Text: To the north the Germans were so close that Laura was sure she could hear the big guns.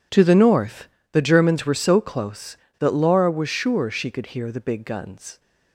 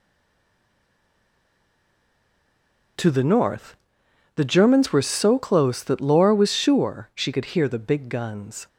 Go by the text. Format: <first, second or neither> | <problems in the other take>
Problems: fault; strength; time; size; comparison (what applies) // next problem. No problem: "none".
first | stays silent before the first word; strong; until 2.9 s; 2.9 s long // pauses between "north" and "the"; noticeable; at 3.7 s; 0.60 s long; slight in the first